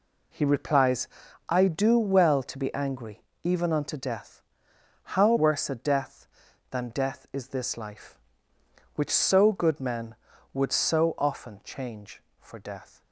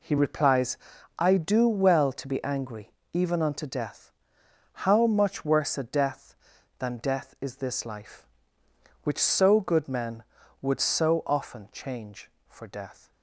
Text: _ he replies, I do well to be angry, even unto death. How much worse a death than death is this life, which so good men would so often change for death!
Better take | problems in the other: second | skips "much"; at 5.3 s

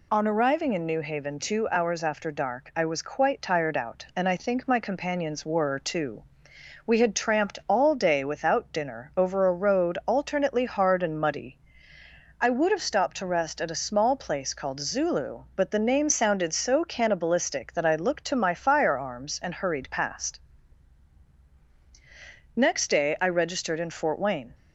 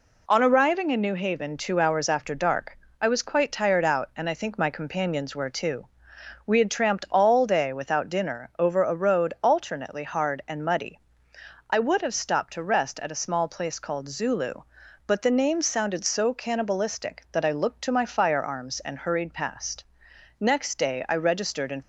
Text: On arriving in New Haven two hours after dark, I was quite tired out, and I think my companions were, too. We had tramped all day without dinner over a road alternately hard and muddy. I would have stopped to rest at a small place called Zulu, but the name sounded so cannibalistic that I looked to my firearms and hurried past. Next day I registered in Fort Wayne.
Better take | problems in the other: first | stops before "Fort Wayne"; at 21.8 s

